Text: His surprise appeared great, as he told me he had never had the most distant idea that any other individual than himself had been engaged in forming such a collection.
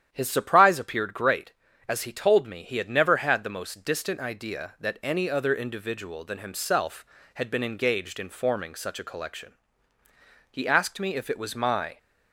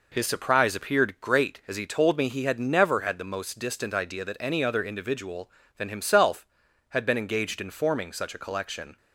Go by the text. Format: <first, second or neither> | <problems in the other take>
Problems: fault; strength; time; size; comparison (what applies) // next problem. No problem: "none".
second | starts louder than the rest; strong; until 1.1 s; 10 dB // goes on to say "He asked me if it was my"; from 10.4 s on; 1.4 s long